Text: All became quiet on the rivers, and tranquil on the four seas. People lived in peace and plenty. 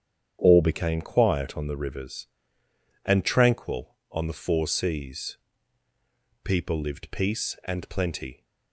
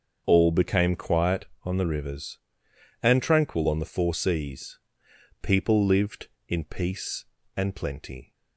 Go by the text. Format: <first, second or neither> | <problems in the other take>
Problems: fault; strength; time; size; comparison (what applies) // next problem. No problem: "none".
second | starts louder than the rest; strong; until 1.4 s; 8.5 dB; also in the second // skips "in"; at 7.0 s